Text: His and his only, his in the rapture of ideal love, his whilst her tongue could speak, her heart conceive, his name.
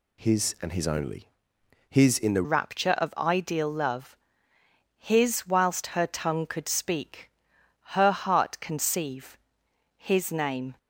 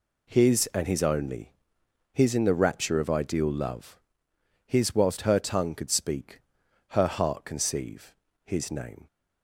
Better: second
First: changes voice at "rapture"; from 2.4 s on; 8.3 s long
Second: none

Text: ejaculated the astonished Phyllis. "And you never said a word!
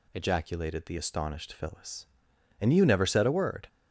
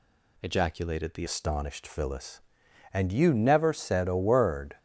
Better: first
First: none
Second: changes voice at "astonished"; from 1.2 s on; 3.5 s long

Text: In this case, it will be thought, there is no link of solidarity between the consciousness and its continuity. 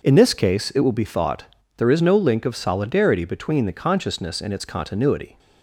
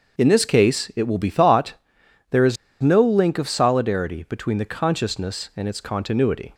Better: first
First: none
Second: starts louder than the rest; until 1.2 s; 6.5 dB // pauses between "is" and "no"; slight; at 2.5 s; 0.25 s long

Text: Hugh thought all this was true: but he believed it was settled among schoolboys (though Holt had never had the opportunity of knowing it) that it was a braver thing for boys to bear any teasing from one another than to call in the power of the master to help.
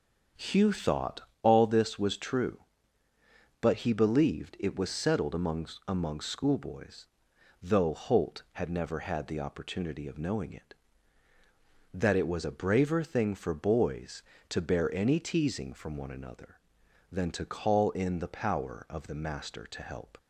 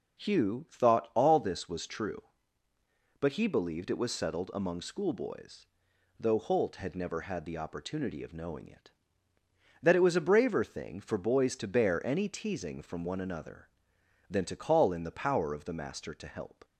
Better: second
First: starts louder than the rest; until 1.5 s; 7 dB // pauses between "thought" and "all"; slight; at 1.2 s; 0.22 s long // says "among" twice; at 5.8 s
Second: none

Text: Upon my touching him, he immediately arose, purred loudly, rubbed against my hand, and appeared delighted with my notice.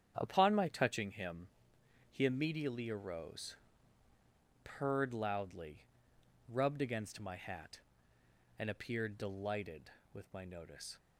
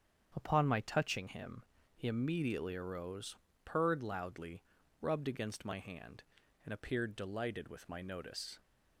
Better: second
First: starts louder than the rest; strong; until 1.1 s; 8.5 dB // says "hat" for "hand"; at 7.3 s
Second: starts louder than the rest; strong; until 1.3 s; 8 dB

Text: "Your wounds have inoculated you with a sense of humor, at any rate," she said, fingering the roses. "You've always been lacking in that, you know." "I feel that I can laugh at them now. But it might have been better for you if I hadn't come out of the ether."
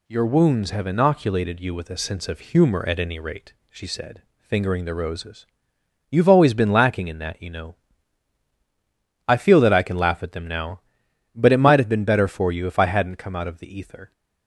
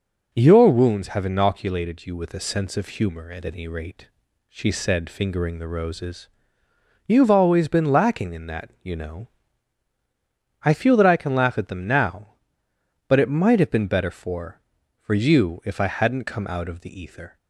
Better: first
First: none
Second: says "for" twice; at 15.0 s

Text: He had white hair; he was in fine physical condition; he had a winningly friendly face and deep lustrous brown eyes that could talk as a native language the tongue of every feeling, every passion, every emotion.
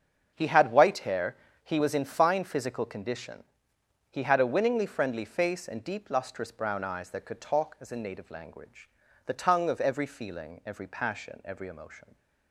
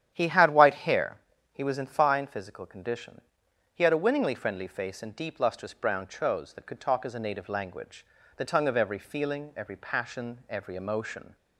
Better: first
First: starts louder than the rest; strong; until 1.3 s; 7 dB // pauses between "language" and "the"; slight; at 8.8 s; 0.36 s long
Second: starts louder than the rest; strong; until 1.1 s; 10 dB // says "chose" for "eyes"; at 6.0 s // pauses between "language" and "the"; slight; at 8.0 s; 0.30 s long

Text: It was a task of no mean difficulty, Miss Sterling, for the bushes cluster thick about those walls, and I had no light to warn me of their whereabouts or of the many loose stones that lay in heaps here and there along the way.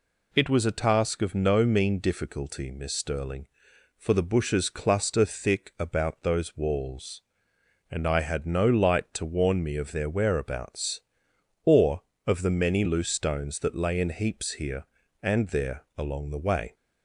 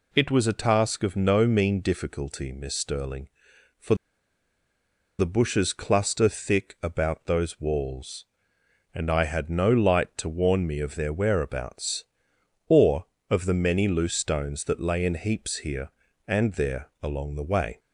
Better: first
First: none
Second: pauses between "for" and "the"; at 3.9 s; 1.2 s long

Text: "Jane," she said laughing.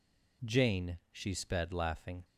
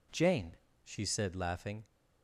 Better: second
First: says "sped" for "said"; at 1.3 s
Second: none

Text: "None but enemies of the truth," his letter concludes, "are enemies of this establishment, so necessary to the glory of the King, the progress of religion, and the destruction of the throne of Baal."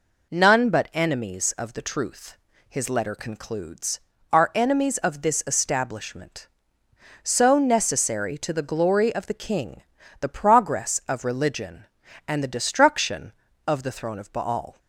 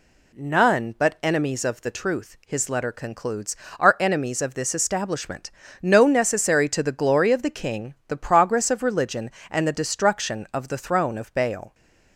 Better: first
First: none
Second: says "no" for "so"; at 5.8 s

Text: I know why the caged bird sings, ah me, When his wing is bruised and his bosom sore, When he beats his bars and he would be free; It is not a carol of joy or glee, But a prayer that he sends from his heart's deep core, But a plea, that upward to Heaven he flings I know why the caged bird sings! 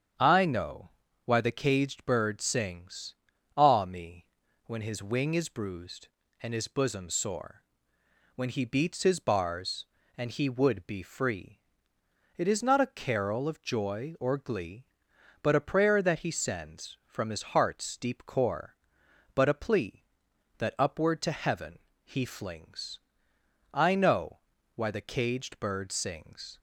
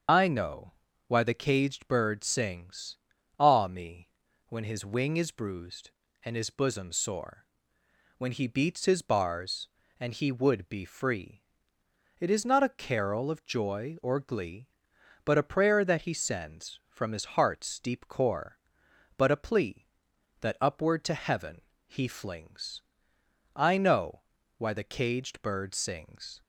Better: first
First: starts louder than the rest; strong; until 1.5 s; 8 dB // pauses between "know" and "why"; at 0.8 s; 0.38 s long // pauses between "Heaven" and "he"; slight; at 21.7 s; 0.28 s long // pauses between "flings" and "I"; noticeable; at 22.9 s; 0.72 s long // pauses between "know" and "why"; at 24.3 s; 0.38 s long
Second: loses the start of "I"; at 0.0 s; 80 ms // starts louder than the rest; until 1.4 s; 7 dB // pauses between "know" and "why"; at 0.7 s; 0.38 s long // pauses between "Heaven" and "he"; slight; at 21.6 s; 0.28 s long // pauses between "flings" and "I"; noticeable; at 22.8 s; 0.72 s long // pauses between "know" and "why"; at 24.2 s; 0.38 s long

